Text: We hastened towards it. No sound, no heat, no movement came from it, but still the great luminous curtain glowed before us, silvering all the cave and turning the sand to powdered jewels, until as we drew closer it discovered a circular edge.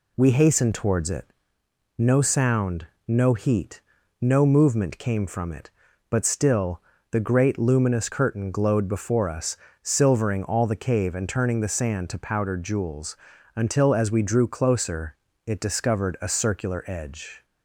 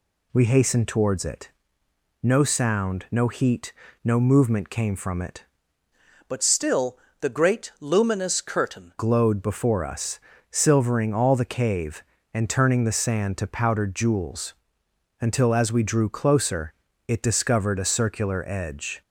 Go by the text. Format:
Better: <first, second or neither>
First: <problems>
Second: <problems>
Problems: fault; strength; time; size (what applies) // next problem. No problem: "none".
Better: first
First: pauses between "still" and "the"; slight; at 6.8 s; 0.30 s long // pauses between "closer" and "it"; slight; at 15.1 s; 0.32 s long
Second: changes voice from "but" to "curtain"; from 6.2 to 8.9 s; 2.7 s long // pauses between "still" and "the"; slight; at 6.9 s; 0.22 s long // pauses between "closer" and "it"; slight; at 16.7 s; 0.34 s long